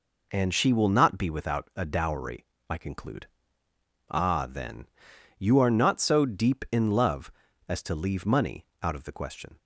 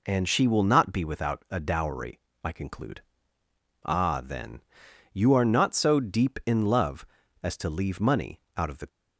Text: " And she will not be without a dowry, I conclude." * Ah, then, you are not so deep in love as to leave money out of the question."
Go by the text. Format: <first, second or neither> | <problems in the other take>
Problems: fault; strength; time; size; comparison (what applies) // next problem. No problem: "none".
first | pauses between "money" and "out"; slight; at 8.3 s; 0.16 s long; slight in the first // stops before "question"; at 8.8 s